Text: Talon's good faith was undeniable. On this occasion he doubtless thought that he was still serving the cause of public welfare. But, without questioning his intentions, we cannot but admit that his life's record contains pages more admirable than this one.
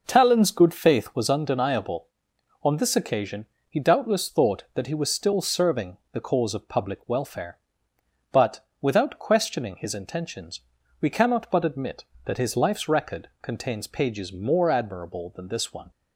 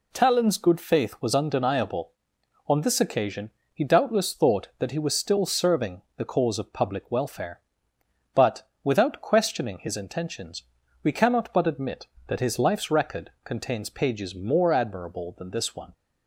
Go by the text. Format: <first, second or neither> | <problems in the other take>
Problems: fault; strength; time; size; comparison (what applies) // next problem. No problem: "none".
second | starts louder than the rest; noticeable; until 1.4 s; 5.5 dB // pauses between "occasion" and "he"; slight; at 3.4 s; 0.22 s long; slight in the second // pauses between "serving" and "the"; slight; at 5.9 s; 0.16 s long; slight in the second